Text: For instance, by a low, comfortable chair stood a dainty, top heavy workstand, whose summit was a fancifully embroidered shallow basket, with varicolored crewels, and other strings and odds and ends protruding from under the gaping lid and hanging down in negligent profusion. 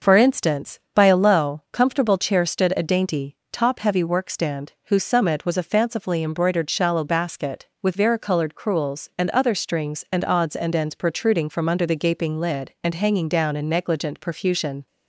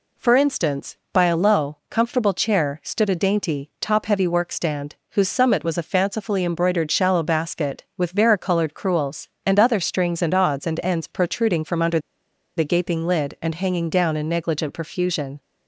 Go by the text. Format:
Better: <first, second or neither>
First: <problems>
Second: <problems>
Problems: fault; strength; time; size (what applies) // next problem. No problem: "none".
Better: first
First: none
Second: pauses between "under" and "the"; noticeable; at 11.9 s; 0.58 s long